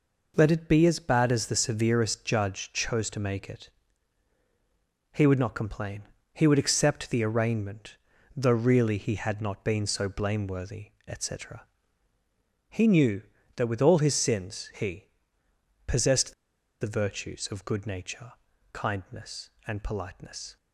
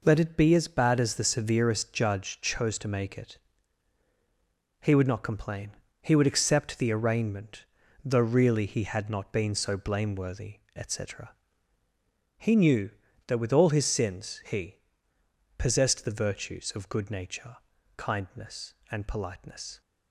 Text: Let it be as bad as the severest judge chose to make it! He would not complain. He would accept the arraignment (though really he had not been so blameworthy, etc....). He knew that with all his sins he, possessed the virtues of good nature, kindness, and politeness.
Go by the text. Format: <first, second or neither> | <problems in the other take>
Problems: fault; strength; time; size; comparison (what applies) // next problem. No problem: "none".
second | pauses between "possessed" and "the"; noticeable; at 16.3 s; 0.47 s long